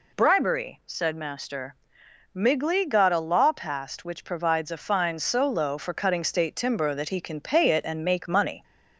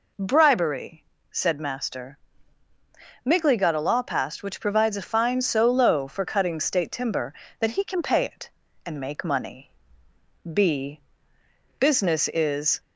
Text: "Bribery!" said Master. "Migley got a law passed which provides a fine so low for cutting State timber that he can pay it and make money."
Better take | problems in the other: first | goes on to say "B Business is"; strong; from 10.4 s on; 2.3 s long

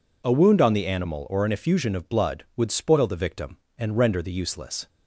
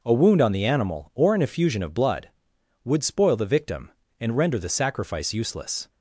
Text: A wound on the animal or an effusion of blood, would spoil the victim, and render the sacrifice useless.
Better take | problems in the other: second | skips "sacrifice"; at 4.3 s

